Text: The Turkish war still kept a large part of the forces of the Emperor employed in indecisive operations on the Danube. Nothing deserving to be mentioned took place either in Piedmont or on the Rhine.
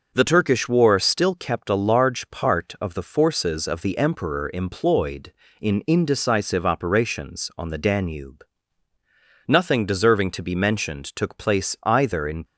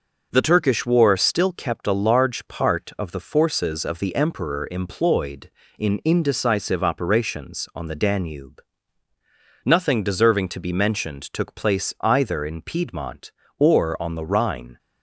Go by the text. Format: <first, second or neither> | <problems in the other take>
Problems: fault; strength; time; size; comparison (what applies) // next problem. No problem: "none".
second | stops before "Piedmont or on the Rhine"; at 12.4 s